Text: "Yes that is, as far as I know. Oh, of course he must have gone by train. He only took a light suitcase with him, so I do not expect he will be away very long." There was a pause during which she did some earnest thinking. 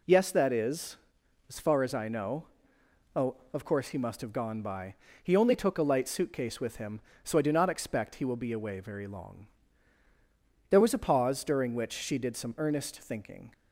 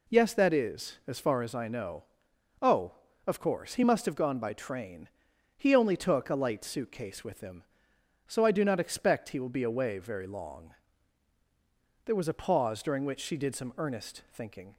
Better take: second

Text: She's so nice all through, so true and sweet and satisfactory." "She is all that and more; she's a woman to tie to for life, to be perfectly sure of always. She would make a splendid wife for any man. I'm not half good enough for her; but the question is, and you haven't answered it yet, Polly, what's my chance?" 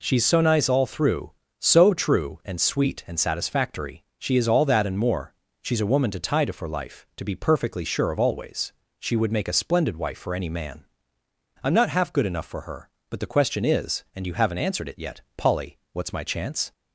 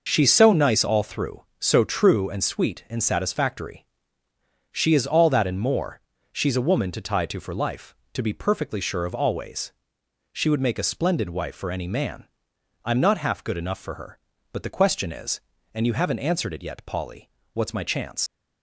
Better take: first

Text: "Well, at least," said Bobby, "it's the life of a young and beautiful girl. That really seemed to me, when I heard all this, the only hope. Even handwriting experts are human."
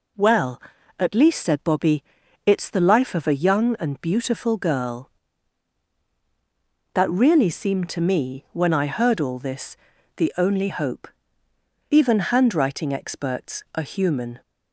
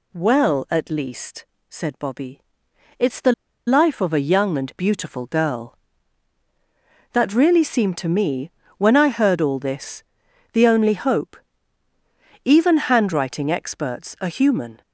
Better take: first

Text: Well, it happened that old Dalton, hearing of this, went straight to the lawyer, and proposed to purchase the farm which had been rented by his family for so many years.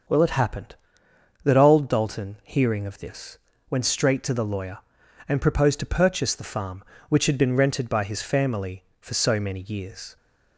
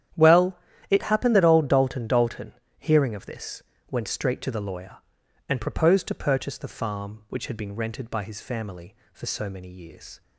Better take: first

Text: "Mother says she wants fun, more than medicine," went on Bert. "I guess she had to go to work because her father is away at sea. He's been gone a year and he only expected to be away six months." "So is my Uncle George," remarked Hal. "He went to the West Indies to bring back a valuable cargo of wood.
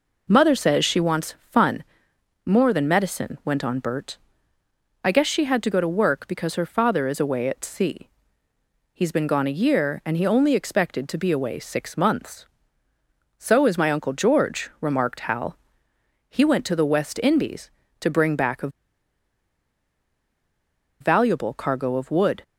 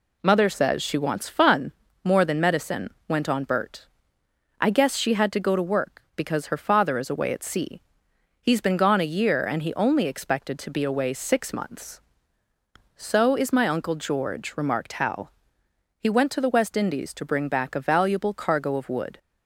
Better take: second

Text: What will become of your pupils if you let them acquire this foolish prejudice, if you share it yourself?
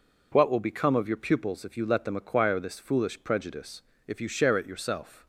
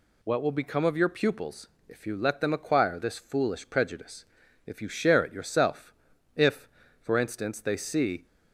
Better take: first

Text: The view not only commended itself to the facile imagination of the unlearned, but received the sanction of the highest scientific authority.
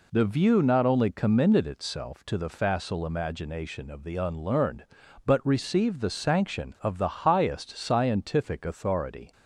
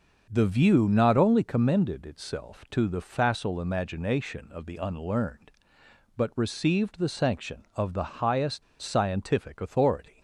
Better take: first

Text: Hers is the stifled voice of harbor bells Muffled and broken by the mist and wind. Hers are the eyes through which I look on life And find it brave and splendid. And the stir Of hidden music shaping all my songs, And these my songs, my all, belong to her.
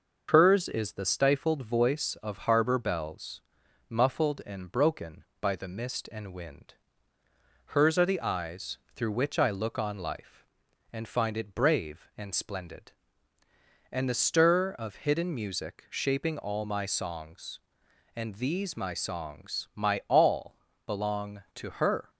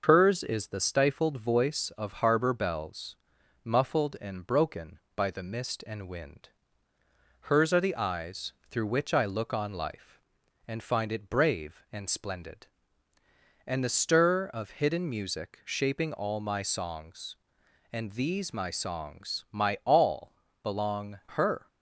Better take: first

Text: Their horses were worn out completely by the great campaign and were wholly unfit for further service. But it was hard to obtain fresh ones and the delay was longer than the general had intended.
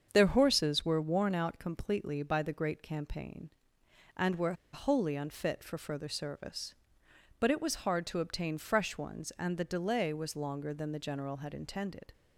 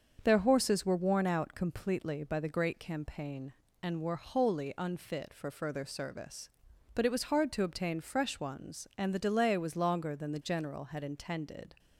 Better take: second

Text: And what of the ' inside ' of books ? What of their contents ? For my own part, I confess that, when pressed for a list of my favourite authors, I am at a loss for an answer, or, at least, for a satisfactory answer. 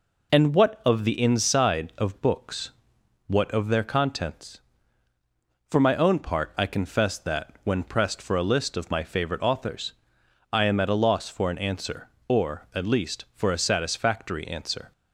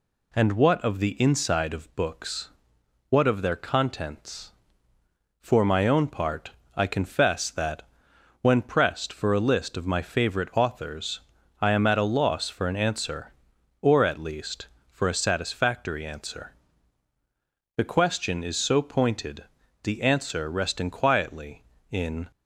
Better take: first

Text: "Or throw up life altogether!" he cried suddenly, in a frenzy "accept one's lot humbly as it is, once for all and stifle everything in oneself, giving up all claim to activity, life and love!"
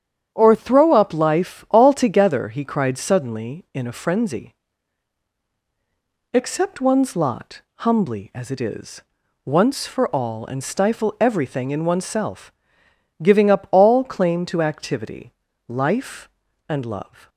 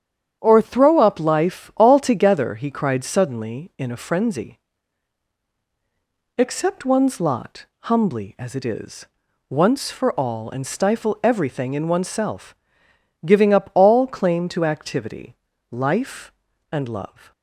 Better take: neither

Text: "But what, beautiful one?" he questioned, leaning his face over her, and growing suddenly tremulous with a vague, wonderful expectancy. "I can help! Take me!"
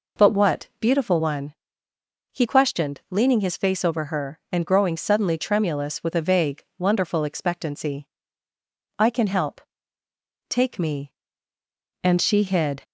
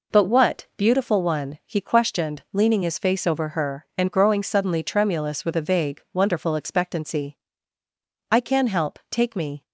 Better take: second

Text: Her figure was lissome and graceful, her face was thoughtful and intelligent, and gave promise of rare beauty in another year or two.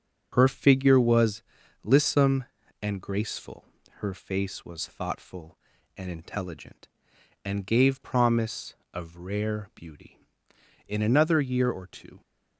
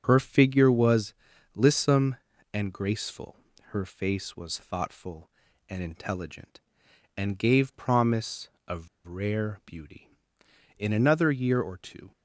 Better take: first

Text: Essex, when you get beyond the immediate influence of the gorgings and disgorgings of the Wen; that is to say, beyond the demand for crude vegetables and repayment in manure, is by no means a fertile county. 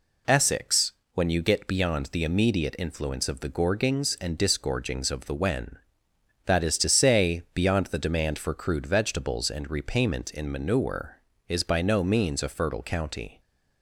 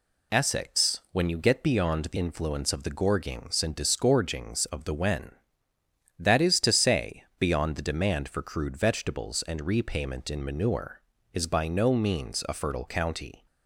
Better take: first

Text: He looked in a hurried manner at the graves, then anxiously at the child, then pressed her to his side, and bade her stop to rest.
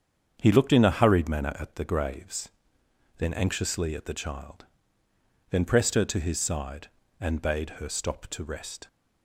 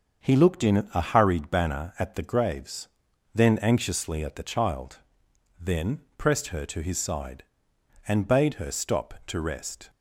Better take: first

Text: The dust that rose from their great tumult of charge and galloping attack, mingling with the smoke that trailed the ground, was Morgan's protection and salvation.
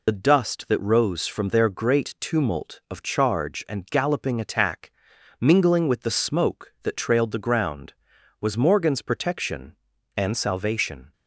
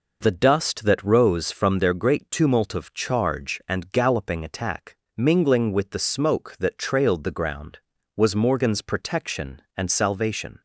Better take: second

